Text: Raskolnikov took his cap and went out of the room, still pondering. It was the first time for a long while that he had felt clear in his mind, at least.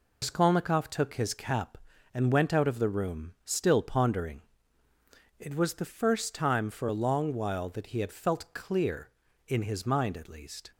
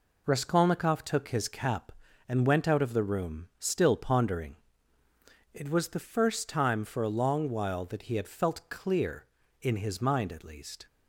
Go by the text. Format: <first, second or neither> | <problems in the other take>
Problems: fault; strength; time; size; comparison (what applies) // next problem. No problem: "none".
second | loses the start of "Raskolnikov"; at 0.2 s; 105 ms